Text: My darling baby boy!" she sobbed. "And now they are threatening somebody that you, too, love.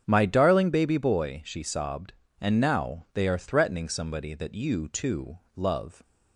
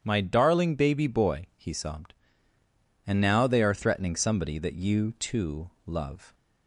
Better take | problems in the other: first | starts louder than the rest; strong; until 1.0 s; 9 dB; strong in the first // says "he" for "she"; at 1.5 s

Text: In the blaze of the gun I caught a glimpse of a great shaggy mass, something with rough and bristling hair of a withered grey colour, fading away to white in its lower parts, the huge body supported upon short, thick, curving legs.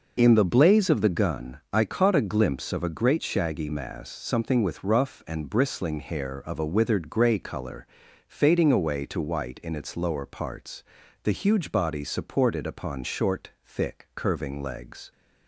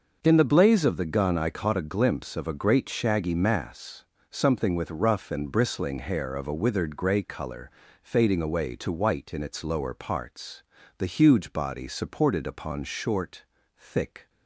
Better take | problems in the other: first | starts louder than the rest; noticeable; until 1.2 s; 6 dB // stops before "curving legs"; at 14.2 s

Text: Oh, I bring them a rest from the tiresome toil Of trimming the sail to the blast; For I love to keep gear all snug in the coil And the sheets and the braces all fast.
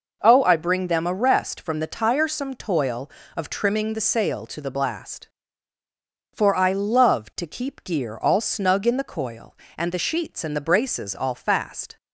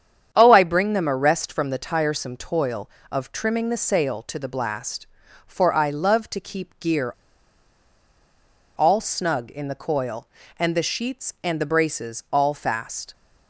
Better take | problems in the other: first | starts louder than the rest; strong; until 1.3 s; 8.5 dB // pauses between "gear" and "all"; strong; at 7.1 s; 1.6 s long

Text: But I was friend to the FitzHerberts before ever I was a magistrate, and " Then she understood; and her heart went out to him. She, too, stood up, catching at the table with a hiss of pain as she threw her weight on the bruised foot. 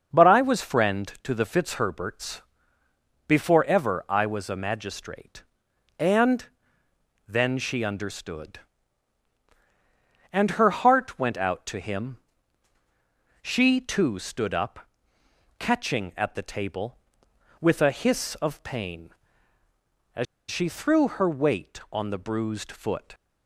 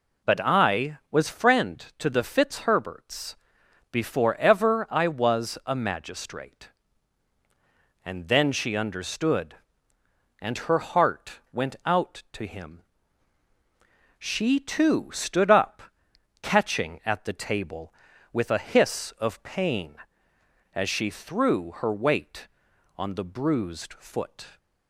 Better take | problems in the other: second | starts louder than the rest; until 1.2 s; 7 dB // pauses between "FitzHerberts" and "before"; noticeable; at 2.4 s; 0.86 s long; noticeable in the second // pauses between "as" and "she"; slight; at 20.2 s; 0.25 s long

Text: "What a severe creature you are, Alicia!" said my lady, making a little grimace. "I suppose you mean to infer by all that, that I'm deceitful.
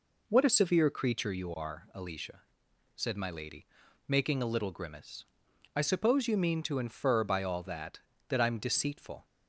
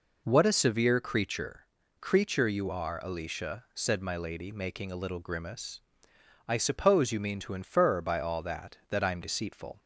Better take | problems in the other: first | says "creature" twice; at 1.9 s

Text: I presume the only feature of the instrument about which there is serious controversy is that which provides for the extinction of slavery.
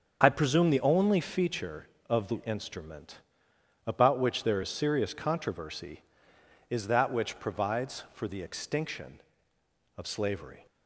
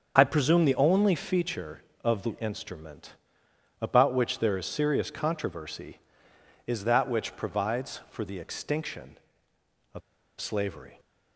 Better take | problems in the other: first | starts louder than the rest; until 1.2 s; 6 dB; also in the first // pauses between "instrument" and "about"; noticeable; at 3.1 s; 0.66 s long; noticeable in the first // pauses between "of" and "slavery"; at 10.0 s; 0.38 s long

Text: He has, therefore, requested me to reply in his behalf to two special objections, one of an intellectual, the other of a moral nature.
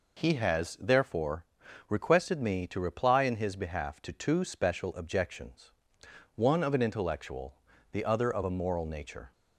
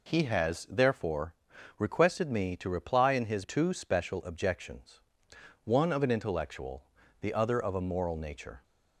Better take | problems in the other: first | skips "behalf to"; at 3.4 s

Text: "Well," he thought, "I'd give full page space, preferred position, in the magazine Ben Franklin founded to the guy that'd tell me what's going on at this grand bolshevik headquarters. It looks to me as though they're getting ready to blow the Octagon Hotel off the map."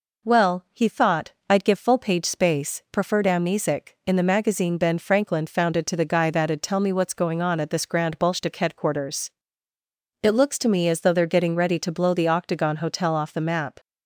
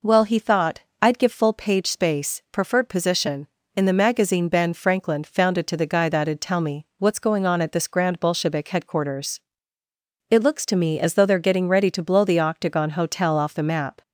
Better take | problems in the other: second | says "amnesic" for "position"; at 3.2 s

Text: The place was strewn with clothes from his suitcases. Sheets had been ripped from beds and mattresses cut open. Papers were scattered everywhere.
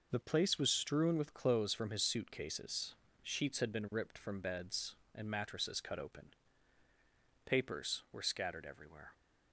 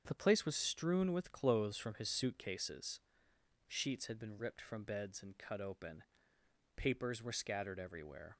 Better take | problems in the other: first | starts louder than the rest; until 1.0 s; 7 dB // skips "mattresses"; at 5.3 s

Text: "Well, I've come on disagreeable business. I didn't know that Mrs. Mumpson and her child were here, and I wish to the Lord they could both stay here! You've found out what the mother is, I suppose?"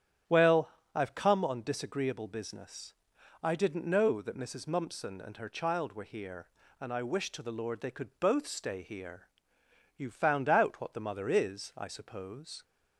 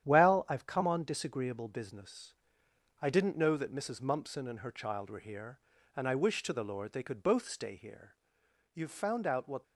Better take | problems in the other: first | starts louder than the rest; strong; until 1.1 s; 10 dB; strong in the first // stops before "the mother is I suppose"; at 9.6 s

